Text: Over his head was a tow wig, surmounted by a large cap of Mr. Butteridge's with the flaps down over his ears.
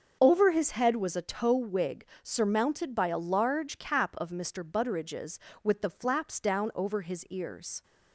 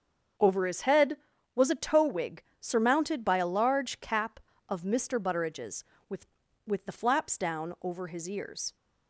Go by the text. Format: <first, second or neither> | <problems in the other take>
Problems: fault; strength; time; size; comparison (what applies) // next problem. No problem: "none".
first | starts louder than the rest; strong; until 1.7 s; 7 dB; also in the first // says "with" twice; at 6.6 s